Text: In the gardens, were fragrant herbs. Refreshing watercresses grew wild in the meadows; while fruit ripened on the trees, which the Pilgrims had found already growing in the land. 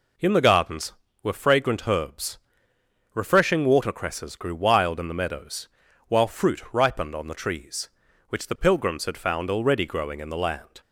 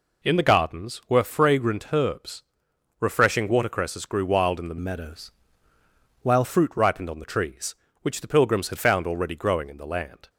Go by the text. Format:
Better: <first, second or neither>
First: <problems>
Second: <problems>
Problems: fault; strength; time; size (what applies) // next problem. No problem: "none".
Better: first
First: none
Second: changes voice from "meadows" to "while"; from 4.7 to 6.4 s; 1.7 s long